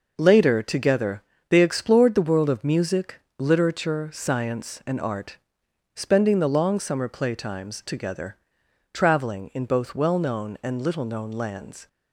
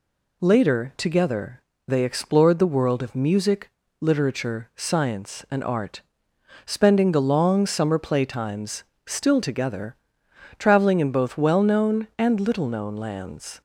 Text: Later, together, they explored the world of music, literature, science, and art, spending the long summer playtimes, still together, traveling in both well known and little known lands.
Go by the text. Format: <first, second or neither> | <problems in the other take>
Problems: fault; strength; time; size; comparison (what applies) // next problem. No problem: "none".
second | skips "still"; at 7.8 s